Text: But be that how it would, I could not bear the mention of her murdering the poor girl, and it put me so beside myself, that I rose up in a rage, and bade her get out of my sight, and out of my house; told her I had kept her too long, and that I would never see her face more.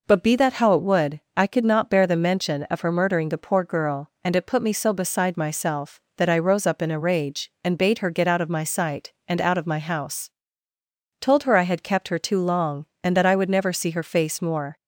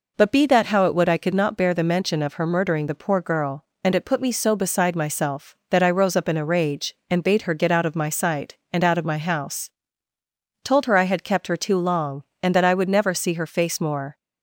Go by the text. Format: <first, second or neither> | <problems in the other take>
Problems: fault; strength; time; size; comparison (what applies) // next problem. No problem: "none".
neither | none